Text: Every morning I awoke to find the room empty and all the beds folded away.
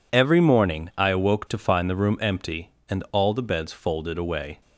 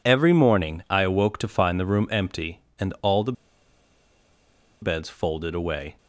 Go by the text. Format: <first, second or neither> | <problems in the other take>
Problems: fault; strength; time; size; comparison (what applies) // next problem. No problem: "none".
first | pauses between "the" and "beds"; strong; at 3.3 s; 1.4 s long